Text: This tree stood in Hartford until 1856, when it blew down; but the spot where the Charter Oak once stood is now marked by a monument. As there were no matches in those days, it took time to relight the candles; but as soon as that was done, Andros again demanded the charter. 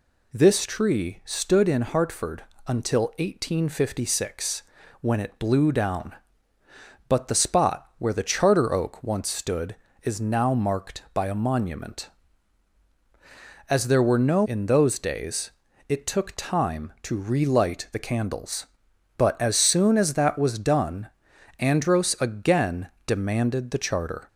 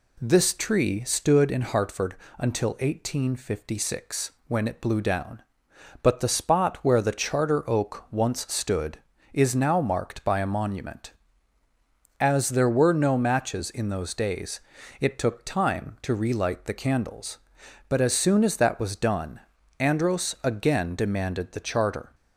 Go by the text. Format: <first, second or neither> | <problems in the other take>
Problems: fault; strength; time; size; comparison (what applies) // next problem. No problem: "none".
second | pauses between "Hartford" and "until"; slight; at 2.4 s; 0.24 s long; slight in the second // skips "matches"; at 14.4 s // pauses between "again" and "demanded"; slight; at 22.8 s; 0.16 s long